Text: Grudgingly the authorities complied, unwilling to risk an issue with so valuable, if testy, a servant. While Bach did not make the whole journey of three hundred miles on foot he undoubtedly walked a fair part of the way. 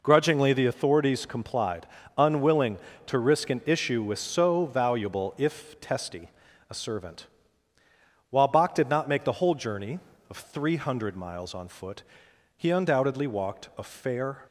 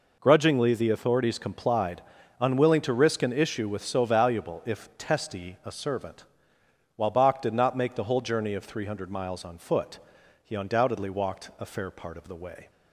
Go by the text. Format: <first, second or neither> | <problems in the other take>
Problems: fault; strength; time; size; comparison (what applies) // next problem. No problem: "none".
second | pauses between "foot" and "he"; noticeable; at 12.0 s; 0.52 s long; also in the second // stops before "part of the way"; at 14.4 s